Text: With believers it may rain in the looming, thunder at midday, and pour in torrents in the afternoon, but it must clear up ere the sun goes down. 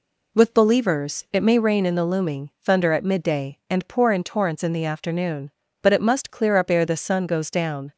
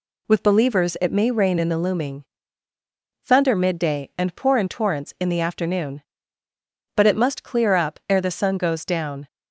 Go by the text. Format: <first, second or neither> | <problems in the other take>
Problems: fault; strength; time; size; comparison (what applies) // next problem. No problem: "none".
first | skips "at"; at 3.5 s